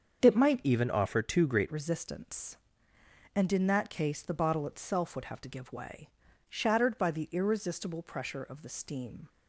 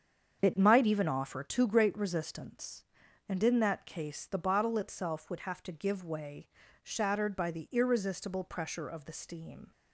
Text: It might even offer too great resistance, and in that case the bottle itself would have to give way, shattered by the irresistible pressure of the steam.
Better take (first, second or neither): second